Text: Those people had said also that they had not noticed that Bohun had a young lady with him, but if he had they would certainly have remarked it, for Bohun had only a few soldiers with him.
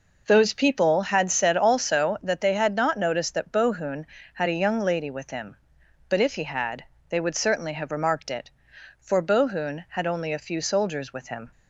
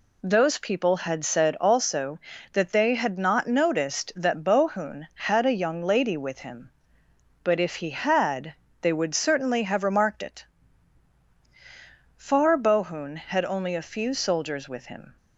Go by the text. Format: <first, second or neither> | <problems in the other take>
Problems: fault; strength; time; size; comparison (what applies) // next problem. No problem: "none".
first | pauses between "had" and "they"; slight; at 8.5 s; 0.26 s long; slight in the first // says "far" for "for"; at 12.1 s